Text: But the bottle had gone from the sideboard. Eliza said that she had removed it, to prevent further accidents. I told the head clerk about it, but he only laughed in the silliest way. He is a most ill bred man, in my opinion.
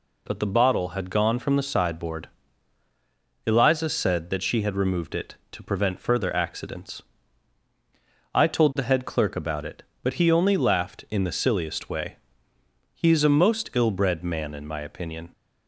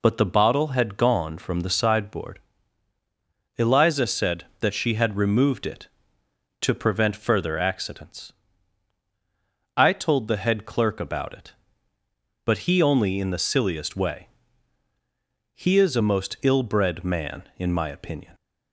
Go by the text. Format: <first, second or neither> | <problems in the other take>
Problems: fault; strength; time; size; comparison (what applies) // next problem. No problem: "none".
first | skips "laughed"; at 13.1 s